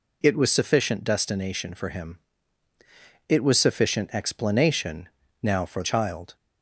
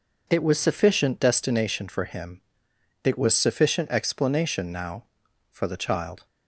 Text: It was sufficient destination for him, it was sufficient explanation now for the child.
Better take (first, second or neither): second